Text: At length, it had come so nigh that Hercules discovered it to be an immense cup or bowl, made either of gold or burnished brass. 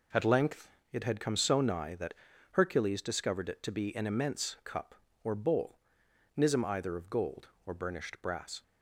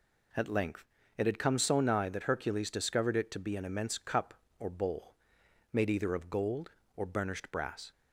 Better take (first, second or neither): second